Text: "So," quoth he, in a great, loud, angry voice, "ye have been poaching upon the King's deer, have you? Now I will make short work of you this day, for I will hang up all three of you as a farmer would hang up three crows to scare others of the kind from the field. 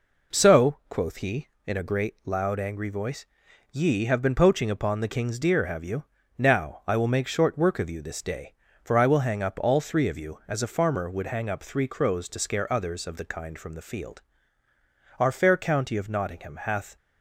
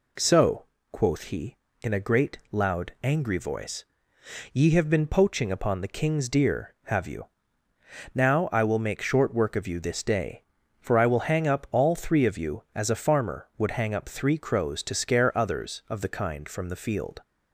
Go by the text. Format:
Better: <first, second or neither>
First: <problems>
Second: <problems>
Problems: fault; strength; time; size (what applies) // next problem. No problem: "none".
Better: second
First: goes on to say "Our fair county of Nottingham hath"; strong; from 15.1 s on; 1.7 s long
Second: none